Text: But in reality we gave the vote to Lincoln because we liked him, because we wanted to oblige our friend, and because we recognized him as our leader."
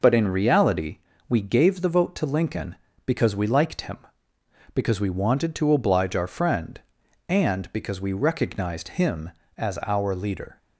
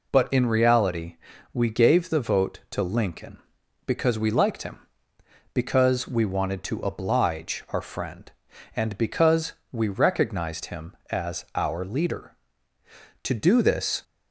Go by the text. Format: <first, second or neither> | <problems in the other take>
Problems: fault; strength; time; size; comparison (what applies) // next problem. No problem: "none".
first | pauses between "reality" and "we"; at 1.1 s; 0.38 s long; slight in the first // pauses between "because" and "we"; slight; at 9.5 s; 0.18 s long // goes on to say "To do this"; noticeable; from 13.2 s on; 0.80 s long